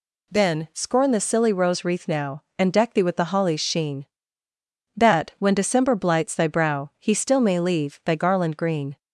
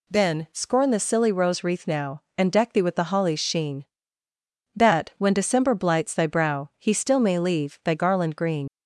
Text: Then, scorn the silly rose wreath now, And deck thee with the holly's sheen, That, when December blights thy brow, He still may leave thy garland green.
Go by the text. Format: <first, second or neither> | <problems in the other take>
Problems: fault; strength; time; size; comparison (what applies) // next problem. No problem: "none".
first | leaves "green" unfinished; at 8.6 s; 95 ms